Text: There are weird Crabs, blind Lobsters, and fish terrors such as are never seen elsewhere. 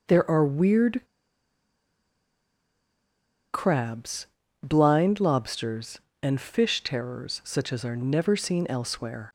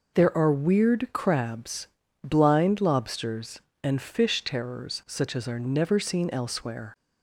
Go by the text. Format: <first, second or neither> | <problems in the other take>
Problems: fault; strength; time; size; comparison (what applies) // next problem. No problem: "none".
second | pauses between "weird" and "Crabs"; strong; at 1.0 s; 2.4 s long